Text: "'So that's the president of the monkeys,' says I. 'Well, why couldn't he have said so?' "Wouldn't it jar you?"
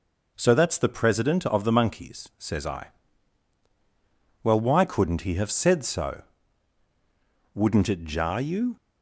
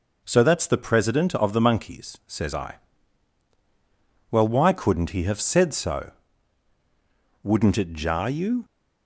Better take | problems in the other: neither | none

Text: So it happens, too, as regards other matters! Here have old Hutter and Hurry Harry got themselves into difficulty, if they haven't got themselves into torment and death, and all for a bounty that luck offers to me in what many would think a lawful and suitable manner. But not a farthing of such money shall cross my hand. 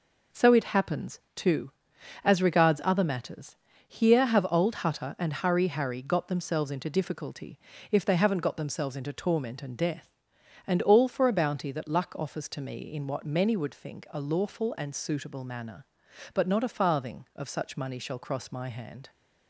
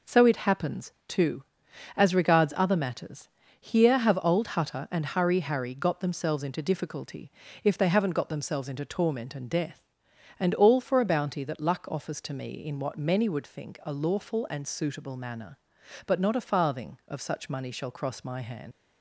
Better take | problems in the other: first | leaves "hand" unfinished; at 18.7 s; 110 ms

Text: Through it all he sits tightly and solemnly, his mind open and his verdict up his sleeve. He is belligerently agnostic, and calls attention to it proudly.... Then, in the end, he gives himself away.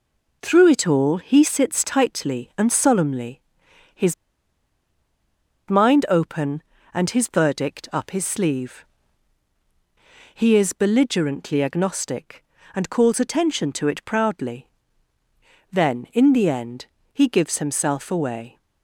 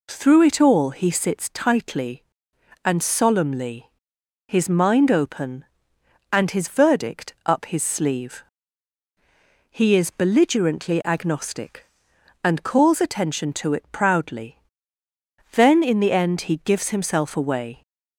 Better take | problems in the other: second | pauses between "his" and "mind"; strong; at 4.1 s; 1.5 s long

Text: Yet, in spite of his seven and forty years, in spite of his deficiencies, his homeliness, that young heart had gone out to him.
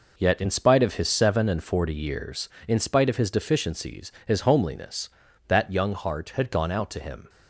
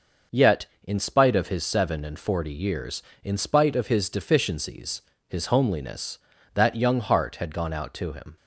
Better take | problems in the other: neither | none

